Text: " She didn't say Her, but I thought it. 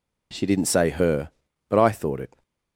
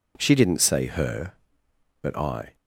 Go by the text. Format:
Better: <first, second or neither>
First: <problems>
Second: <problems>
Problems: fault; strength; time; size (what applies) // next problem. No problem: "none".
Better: first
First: none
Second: stops before "thought it"; at 2.5 s